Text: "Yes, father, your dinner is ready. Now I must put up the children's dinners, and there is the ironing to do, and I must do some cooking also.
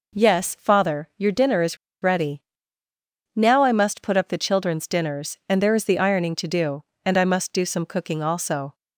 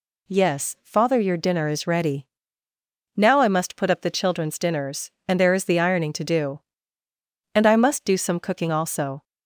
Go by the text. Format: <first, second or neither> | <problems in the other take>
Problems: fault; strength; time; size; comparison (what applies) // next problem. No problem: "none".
second | pauses between "is" and "ready"; slight; at 1.7 s; 0.26 s long